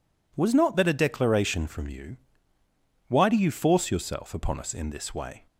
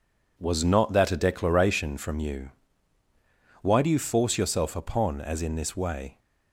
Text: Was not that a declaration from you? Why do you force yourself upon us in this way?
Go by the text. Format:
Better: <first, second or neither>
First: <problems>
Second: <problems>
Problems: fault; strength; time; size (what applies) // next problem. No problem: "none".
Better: first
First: none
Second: says "as" for "us"; at 5.2 s